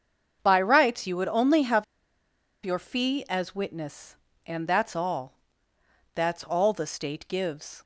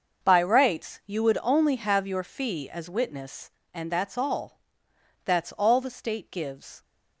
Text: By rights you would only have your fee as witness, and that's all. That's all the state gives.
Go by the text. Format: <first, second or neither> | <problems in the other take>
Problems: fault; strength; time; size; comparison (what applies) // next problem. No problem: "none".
second | starts louder than the rest; until 1.4 s; 7 dB; also in the second // pauses between "have" and "your"; noticeable; at 1.8 s; 0.79 s long